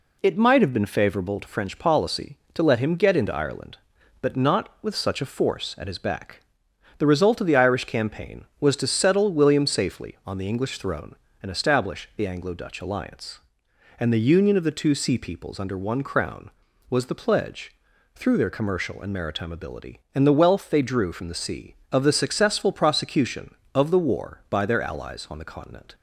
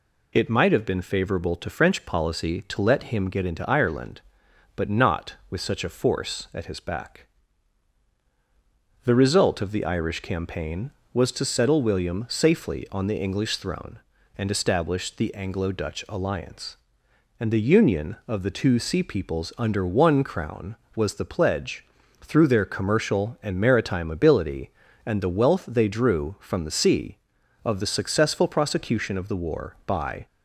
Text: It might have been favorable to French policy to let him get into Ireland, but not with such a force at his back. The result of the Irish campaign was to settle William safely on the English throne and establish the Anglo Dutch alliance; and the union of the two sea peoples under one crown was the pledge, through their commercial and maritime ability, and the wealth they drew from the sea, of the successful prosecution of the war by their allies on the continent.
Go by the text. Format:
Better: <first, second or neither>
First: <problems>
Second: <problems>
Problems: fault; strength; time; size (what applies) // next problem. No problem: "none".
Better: first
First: none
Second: stops before "their allies on the continent"; at 30.2 s